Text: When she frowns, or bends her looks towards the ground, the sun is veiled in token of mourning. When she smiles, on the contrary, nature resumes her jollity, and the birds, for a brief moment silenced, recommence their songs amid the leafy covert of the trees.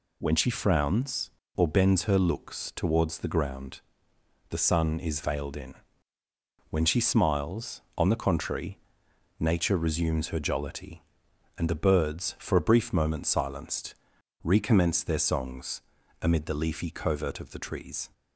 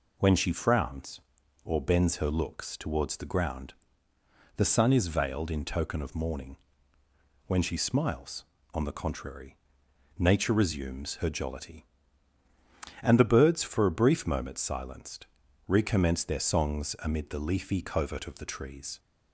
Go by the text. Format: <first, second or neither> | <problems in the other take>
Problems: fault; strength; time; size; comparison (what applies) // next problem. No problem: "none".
second | skips "token of mourning"; at 6.2 s // pauses between "songs" and "amid"; at 15.8 s; 0.40 s long